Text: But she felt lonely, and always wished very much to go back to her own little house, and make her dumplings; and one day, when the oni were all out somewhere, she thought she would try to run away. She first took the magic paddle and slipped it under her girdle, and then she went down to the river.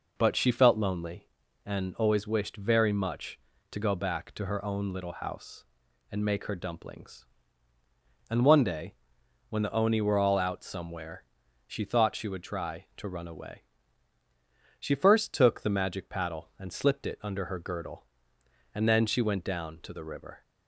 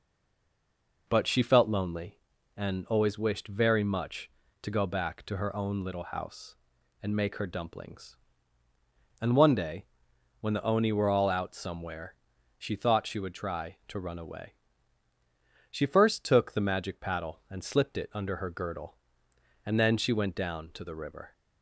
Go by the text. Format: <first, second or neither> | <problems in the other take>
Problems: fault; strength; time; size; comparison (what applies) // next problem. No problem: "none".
first | stays silent before the first word; until 1.0 s; 1.0 s long